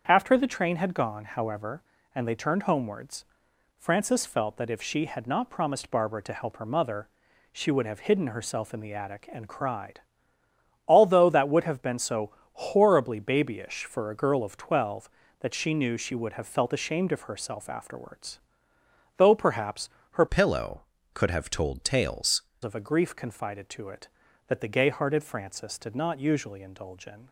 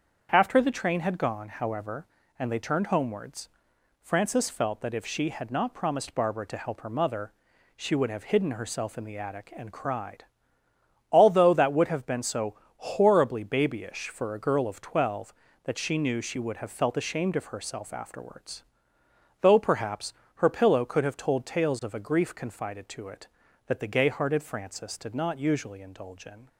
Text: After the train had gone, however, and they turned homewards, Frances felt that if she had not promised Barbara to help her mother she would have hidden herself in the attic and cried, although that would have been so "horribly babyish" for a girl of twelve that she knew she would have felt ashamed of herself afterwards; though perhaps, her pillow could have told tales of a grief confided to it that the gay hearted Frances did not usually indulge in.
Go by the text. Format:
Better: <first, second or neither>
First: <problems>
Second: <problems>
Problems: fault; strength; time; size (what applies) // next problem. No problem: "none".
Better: second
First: starts louder than the rest; until 1.0 s; 7 dB // pauses between "mother" and "she"; at 7.0 s; 0.44 s long // pauses between "so" and "horribly"; slight; at 12.3 s; 0.22 s long // changes voice from "pillow" to "tales"; from 20.2 to 22.4 s; 2.2 s long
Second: starts louder than the rest; until 1.3 s; 7 dB // pauses between "mother" and "she"; at 7.3 s; 0.44 s long // pauses between "so" and "horribly"; slight; at 12.5 s; 0.22 s long